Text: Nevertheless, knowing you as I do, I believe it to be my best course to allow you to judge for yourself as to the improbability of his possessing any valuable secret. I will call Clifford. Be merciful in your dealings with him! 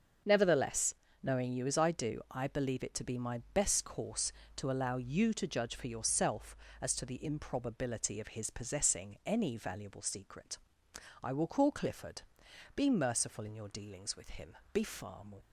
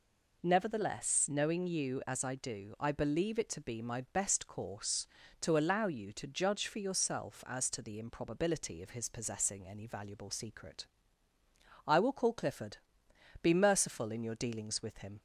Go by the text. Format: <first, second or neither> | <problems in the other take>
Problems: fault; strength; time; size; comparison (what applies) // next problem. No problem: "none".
second | starts louder than the rest; until 1.5 s; 6.5 dB // goes on to say "be far more"; noticeable; from 14.7 s on; 0.64 s long